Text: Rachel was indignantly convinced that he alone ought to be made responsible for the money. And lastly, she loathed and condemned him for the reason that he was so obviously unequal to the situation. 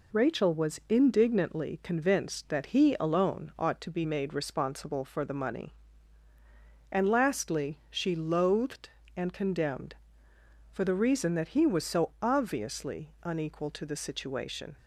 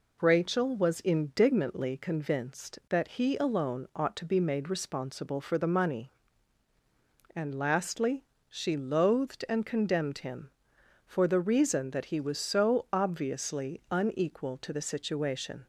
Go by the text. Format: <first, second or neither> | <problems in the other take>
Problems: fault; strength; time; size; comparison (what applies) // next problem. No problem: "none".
second | skips "him"; at 10.3 s